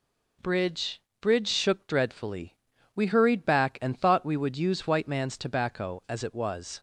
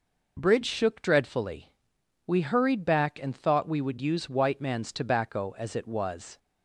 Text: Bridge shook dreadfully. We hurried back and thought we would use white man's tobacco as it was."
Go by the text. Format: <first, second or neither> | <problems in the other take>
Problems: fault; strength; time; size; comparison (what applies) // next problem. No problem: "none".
second | says "Bridge" twice; at 1.1 s